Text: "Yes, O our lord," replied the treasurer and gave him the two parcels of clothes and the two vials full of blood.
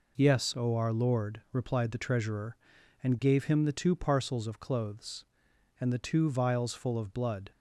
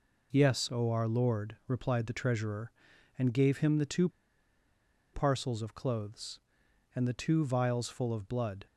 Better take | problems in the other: first | pauses between "two" and "parcels"; at 4.0 s; 1.0 s long

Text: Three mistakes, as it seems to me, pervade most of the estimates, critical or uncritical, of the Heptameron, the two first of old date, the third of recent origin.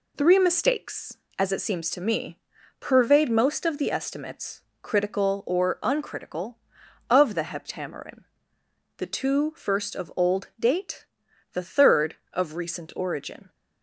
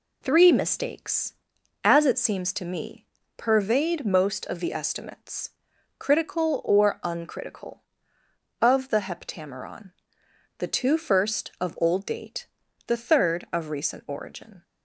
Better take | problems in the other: neither | none

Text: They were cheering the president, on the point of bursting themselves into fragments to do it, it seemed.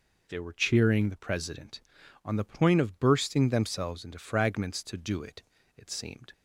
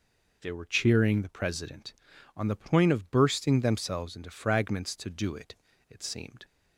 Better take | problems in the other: neither | none

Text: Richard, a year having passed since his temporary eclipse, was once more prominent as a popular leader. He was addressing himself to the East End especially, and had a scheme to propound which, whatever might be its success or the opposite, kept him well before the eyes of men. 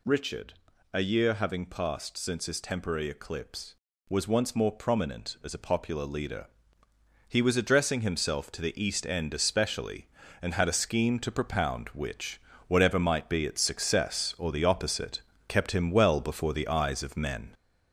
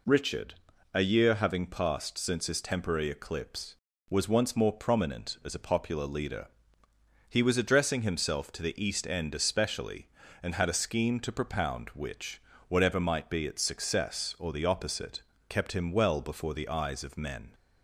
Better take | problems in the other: second | gets louder; noticeable; throughout; 4.5 dB

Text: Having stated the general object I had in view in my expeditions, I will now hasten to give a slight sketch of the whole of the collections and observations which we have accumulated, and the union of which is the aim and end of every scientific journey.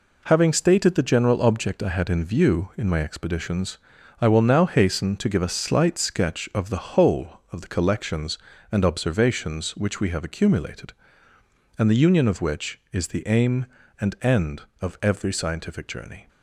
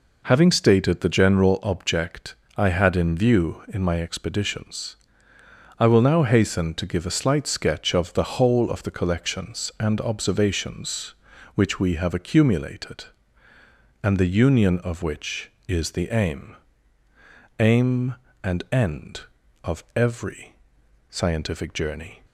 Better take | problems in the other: first | pauses between "object" and "I"; slight; at 2.3 s; 0.22 s long // says "aim" twice; at 17.5 s // pauses between "every" and "scientific"; noticeable; at 20.5 s; 0.56 s long

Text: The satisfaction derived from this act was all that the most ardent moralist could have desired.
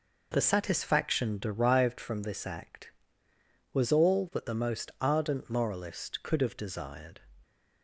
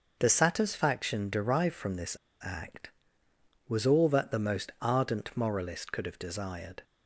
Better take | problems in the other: first | starts louder than the rest; until 1.2 s; 6.5 dB // pauses between "this" and "act"; slight; at 2.1 s; 0.29 s long

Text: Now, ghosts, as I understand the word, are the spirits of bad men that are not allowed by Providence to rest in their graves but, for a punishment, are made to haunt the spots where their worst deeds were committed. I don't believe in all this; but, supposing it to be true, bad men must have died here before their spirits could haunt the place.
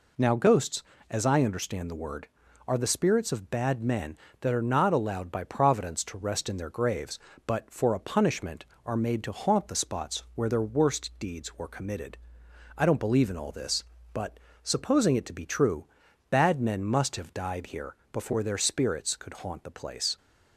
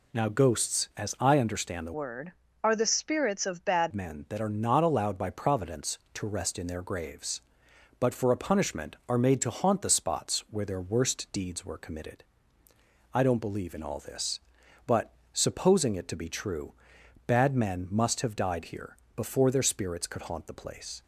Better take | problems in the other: first | changes voice from "word" to "bad"; from 1.9 to 3.9 s; 2.0 s long // pauses between "here" and "before"; slight; at 18.9 s; 0.20 s long; slight in the first

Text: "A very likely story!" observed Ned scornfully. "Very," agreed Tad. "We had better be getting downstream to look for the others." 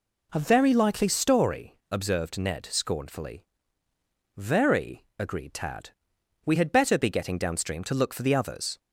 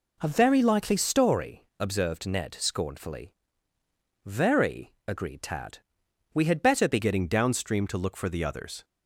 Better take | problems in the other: first | changes voice at "getting"; from 6.9 s on; 1.9 s long

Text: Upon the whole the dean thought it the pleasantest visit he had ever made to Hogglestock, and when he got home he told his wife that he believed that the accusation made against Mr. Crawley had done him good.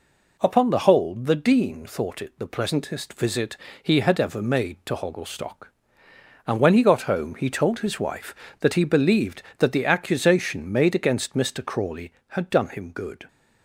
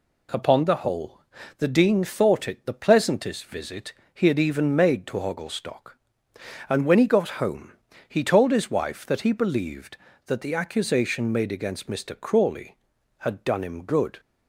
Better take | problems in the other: first | pauses between "whole" and "the"; slight; at 1.2 s; 0.36 s long // pauses between "visit" and "he"; slight; at 3.9 s; 0.20 s long; slight in the first // says "even" for "ever"; at 4.3 s // pauses between "home" and "he"; slight; at 7.7 s; 0.36 s long

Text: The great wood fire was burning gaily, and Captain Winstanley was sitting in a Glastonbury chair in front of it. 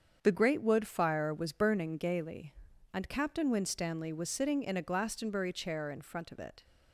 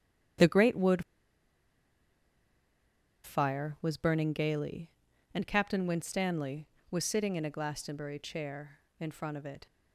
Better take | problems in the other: first | starts louder than the rest; strong; until 3.6 s; 9.5 dB; strong in the first // pauses between "wood" and "fire"; strong; at 1.0 s; 2.2 s long

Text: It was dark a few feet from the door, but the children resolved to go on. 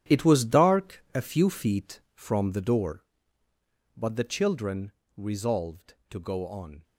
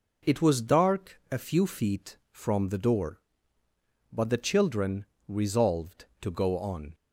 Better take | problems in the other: second | gets quieter; strong; throughout; 11 dB // pauses between "children" and "resolved"; slight; at 4.9 s; 0.22 s long; slight in the second

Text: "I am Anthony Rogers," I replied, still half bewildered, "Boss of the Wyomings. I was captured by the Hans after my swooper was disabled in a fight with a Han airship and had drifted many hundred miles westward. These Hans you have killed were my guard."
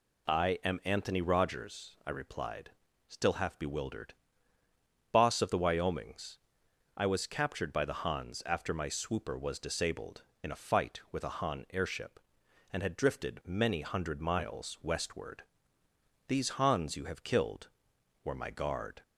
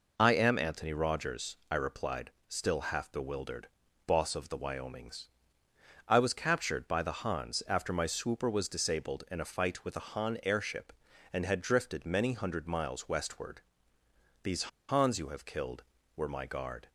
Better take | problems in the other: first | pauses between "These" and "Hans"; slight; at 14.6 s; 0.26 s long

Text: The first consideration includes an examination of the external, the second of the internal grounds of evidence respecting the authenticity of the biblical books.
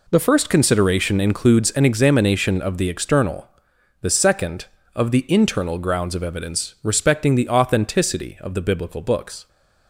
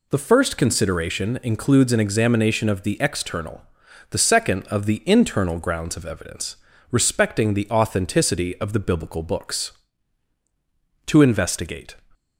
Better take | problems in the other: first | pauses between "evidence" and "respecting"; slight; at 6.5 s; 0.36 s long // goes on to say "To investigate"; noticeable; from 11.0 s on; 0.90 s long

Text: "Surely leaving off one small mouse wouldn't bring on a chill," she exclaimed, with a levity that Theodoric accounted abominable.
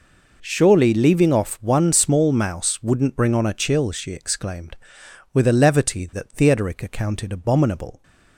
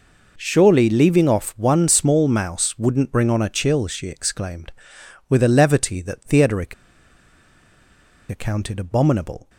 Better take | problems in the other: first | pauses between "Theodoric" and "accounted"; strong; at 6.7 s; 1.5 s long

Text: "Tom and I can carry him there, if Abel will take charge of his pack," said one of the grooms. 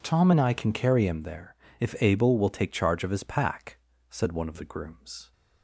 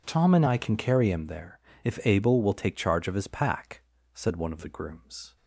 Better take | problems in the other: neither | none

